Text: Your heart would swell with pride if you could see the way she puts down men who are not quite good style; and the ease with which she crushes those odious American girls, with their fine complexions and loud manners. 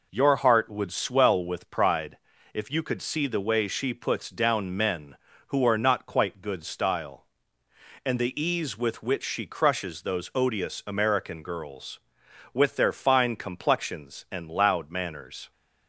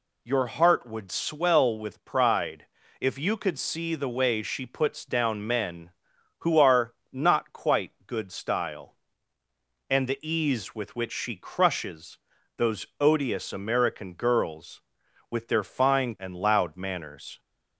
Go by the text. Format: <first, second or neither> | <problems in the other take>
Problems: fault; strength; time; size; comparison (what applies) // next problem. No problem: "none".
first | pauses between "pride" and "if"; slight; at 2.6 s; 0.34 s long; slight in the first // pauses between "are" and "not"; slight; at 6.9 s; 0.20 s long // pauses between "crushes" and "those"; at 12.1 s; 0.40 s long // skips "complexions"; at 16.1 s